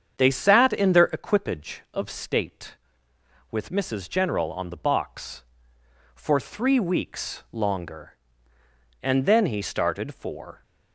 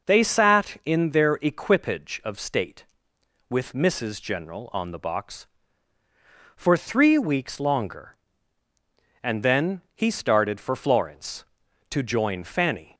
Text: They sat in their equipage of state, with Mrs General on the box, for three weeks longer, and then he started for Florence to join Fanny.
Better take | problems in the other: second | starts louder than the rest; strong; until 1.1 s; 7.5 dB // stops before "Florence to join Fanny"; at 10.6 s

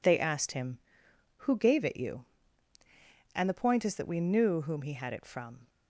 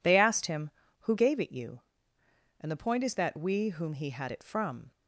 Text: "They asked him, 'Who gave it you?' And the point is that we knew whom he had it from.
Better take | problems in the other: first | skips "knew"; at 3.6 s

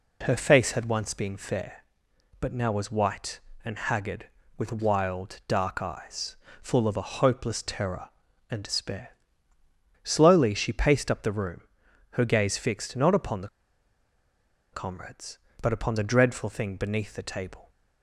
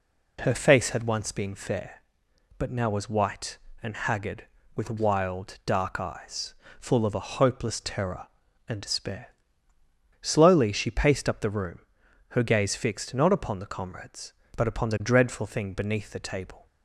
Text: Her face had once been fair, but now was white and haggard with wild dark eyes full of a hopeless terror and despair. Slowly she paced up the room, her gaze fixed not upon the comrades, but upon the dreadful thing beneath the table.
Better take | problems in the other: second | pauses between "eyes" and "full"; slight; at 6.3 s; 0.26 s long; slight in the second // pauses between "the" and "comrades"; strong; at 13.4 s; 1.2 s long

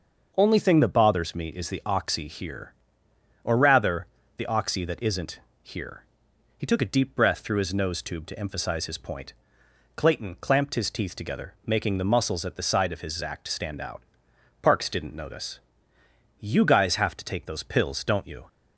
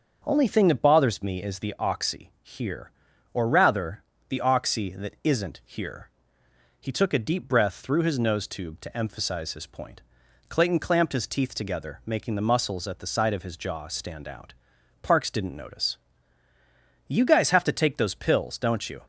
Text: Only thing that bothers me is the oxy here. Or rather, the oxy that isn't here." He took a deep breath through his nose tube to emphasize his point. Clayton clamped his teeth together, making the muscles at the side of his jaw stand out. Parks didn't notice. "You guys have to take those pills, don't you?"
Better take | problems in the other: second | starts louder than the rest; until 1.3 s; 6 dB; also in the second // pauses between "isn't" and "here"; slight; at 5.4 s; 0.20 s long // says "zact" for "jaw"; at 13.2 s

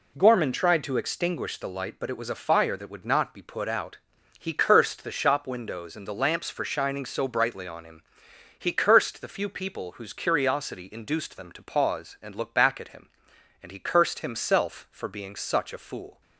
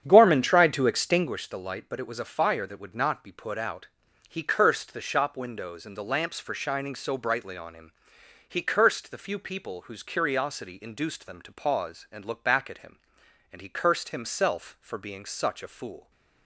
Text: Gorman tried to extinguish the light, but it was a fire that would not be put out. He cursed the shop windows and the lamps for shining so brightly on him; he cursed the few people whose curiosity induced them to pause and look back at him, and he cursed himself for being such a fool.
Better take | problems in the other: first | starts louder than the rest; strong; until 1.3 s; 8.5 dB

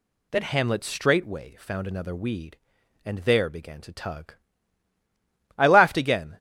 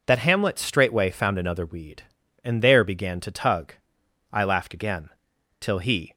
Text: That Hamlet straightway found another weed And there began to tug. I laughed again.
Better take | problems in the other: first | goes on to say "Till he"; from 5.5 s on; 0.54 s long

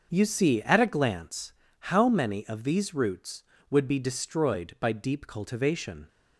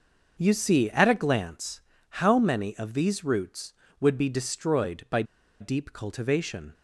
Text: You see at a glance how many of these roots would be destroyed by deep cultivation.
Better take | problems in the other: first | starts louder than the rest; noticeable; until 1.3 s; 6 dB; also in the first // pauses between "glance" and "how"; at 1.8 s; 0.40 s long; also in the first // pauses between "by" and "deep"; at 5.2 s; 0.37 s long

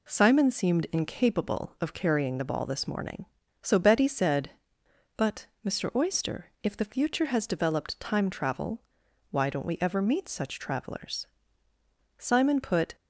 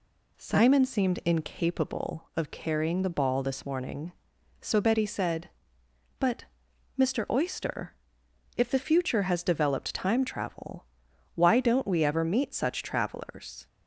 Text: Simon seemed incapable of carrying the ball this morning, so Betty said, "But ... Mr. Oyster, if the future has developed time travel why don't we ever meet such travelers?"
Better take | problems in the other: second | pauses between "travel" and "why"; noticeable; at 8.8 s; 0.50 s long; noticeable in the second // goes on to say "Simon put"; noticeable; from 12.1 s on; 0.78 s long

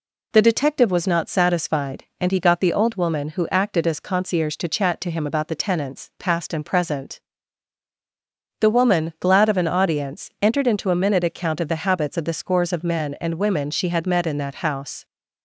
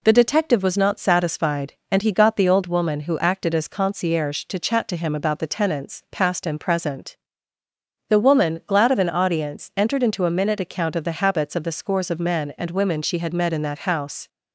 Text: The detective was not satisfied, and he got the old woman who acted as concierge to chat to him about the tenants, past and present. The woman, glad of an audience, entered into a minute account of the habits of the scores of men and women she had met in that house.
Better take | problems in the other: neither | none

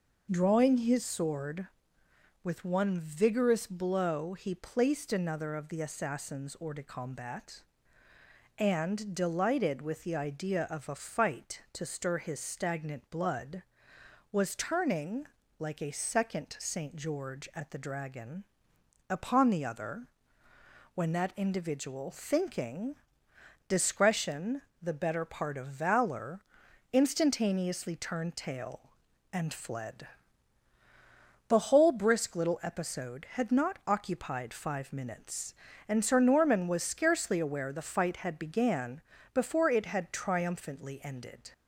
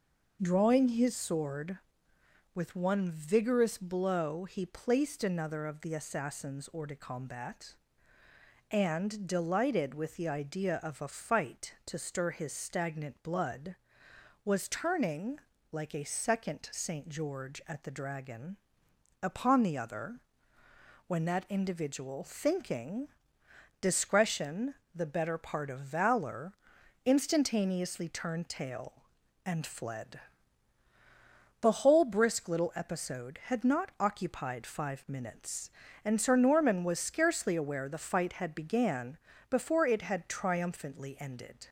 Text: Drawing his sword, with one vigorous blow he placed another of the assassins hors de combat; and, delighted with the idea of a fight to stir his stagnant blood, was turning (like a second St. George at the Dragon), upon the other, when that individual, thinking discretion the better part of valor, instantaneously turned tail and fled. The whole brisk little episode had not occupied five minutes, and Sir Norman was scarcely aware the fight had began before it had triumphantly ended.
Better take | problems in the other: neither | pauses between "thinking" and "discretion"; noticeable; the same in both // pauses between "discretion" and "the"; slight; the same in both // pauses between "began" and "before"; slight; the same in both

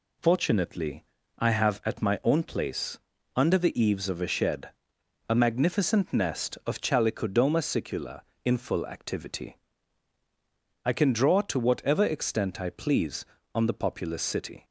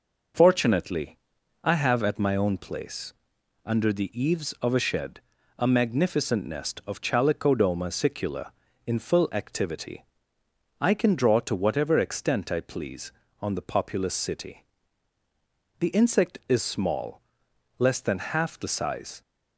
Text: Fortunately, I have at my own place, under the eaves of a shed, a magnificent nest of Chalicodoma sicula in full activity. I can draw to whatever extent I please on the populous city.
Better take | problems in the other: first | goes on to say "The insect is small less than half the size"; strong; from 15.7 s on; 3.4 s long

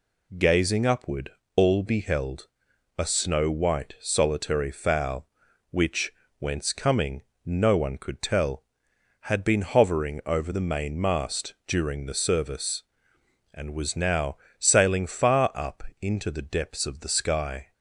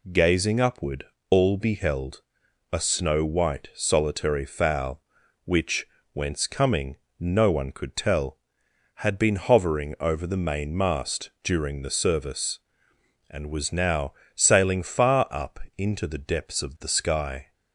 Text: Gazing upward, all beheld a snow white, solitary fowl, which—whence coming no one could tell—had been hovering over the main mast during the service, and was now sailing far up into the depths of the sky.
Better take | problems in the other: neither | pauses between "beheld" and "a"; noticeable; the same in both // pauses between "coming" and "no"; slight; the same in both // pauses between "now" and "sailing"; slight; the same in both // pauses between "up" and "into"; slight; the same in both

